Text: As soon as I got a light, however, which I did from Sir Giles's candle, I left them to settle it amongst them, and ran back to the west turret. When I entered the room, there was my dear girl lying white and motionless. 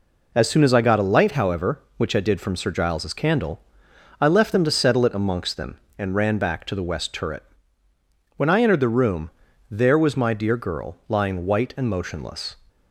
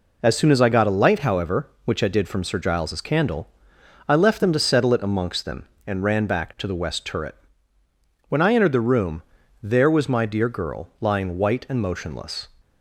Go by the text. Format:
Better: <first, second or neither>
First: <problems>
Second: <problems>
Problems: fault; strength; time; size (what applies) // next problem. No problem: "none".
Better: neither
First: none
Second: none